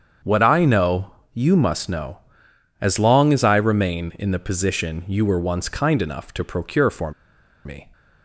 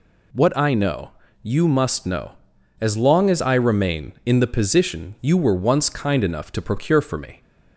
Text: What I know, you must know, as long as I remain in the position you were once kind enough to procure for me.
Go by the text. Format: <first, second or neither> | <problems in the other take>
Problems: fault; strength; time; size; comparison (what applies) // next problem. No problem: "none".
second | starts louder than the rest; strong; until 1.4 s; 7.5 dB // pauses between "for" and "me"; noticeable; at 7.1 s; 0.54 s long